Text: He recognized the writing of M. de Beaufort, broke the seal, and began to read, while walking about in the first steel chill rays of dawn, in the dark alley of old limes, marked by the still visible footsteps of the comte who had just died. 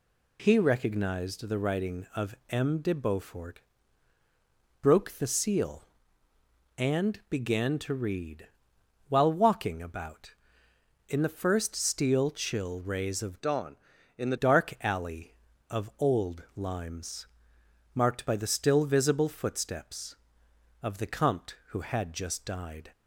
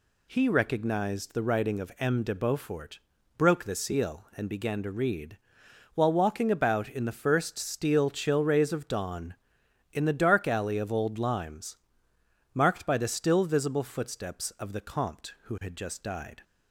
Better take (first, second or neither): second